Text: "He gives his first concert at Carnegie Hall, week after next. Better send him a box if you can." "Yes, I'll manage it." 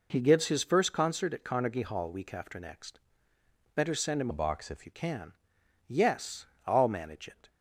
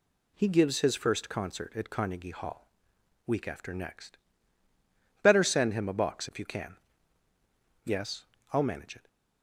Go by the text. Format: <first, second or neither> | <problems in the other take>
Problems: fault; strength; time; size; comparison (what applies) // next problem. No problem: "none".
second | changes voice from "a" to "if"; from 4.2 to 4.8 s; 0.6 s long